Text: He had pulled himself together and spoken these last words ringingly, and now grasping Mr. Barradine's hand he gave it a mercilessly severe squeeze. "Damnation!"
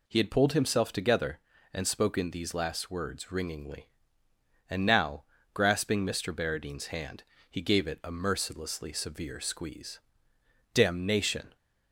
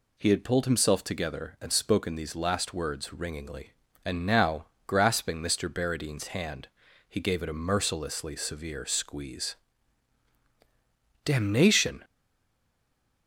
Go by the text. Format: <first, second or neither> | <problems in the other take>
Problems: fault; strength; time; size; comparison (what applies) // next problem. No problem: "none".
first | pauses between "now" and "grasping"; slight; at 4.6 s; 0.22 s long; slight in the first // pauses between "hand" and "he"; at 6.6 s; 0.42 s long; slight in the first // stays silent after the last word; noticeable; from 12.0 s on; 1.2 s long